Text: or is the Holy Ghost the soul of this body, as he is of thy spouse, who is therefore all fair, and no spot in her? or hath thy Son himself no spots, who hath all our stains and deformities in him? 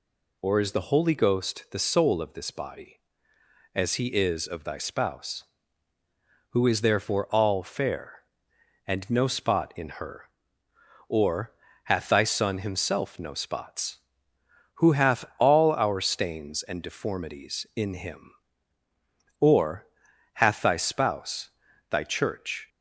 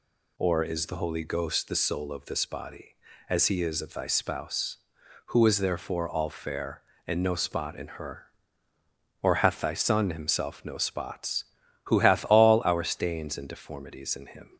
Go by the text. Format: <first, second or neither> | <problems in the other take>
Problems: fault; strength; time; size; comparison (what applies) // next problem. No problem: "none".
second | pauses between "or" and "hath"; slight; at 11.5 s; 0.34 s long // goes on to say "or hath thy spouse thy church"; strong; from 19.4 s on; 3.2 s long